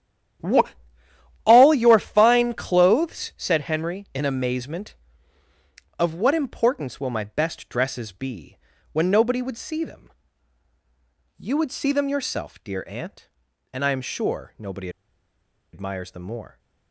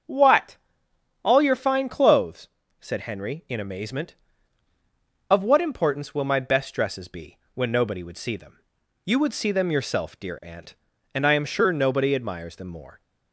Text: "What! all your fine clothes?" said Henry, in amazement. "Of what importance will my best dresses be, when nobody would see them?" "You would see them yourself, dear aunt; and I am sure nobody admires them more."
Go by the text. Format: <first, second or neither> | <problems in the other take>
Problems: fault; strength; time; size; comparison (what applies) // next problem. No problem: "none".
second | starts louder than the rest; strong; until 2.1 s; 10 dB; also in the second // pauses between "nobody" and "admires"; noticeable; at 14.8 s; 0.84 s long